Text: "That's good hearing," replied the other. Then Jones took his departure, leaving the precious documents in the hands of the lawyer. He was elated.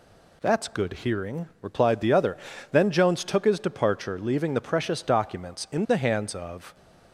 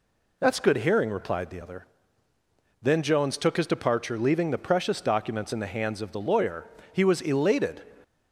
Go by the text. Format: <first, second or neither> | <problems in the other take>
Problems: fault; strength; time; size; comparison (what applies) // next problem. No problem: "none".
second | stops before "the lawyer He was elated"; at 6.7 s